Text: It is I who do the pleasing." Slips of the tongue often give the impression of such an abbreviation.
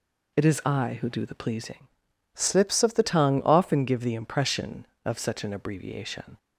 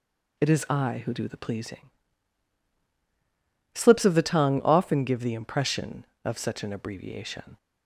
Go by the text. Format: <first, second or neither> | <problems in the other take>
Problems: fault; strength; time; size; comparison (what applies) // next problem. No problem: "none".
second | changes voice from "Slips" to "the"; from 2.3 to 3.0 s; 0.7 s long